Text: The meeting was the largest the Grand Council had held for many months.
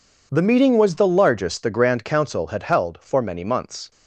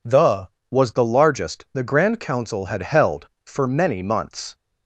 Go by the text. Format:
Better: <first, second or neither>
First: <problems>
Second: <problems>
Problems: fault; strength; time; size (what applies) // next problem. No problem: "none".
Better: first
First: none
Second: skips "meeting"; at 0.5 s